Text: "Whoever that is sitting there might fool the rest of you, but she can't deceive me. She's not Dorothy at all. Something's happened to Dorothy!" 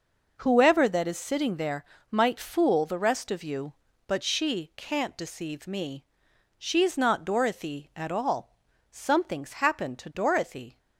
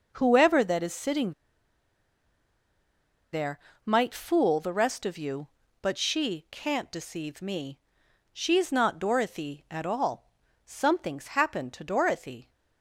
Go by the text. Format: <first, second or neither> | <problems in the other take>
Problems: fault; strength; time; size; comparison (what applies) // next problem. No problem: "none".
first | pauses between "sitting" and "there"; strong; at 1.3 s; 1.9 s long // pauses between "there" and "might"; slight; at 3.5 s; 0.28 s long; slight in the first